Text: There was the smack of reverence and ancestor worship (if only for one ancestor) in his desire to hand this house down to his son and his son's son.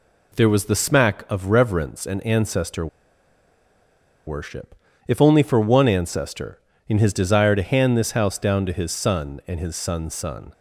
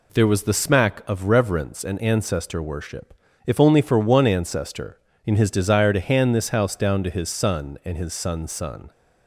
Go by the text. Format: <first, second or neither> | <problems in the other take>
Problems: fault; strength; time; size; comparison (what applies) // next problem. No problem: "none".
second | pauses between "ancestor" and "worship"; strong; at 2.8 s; 1.4 s long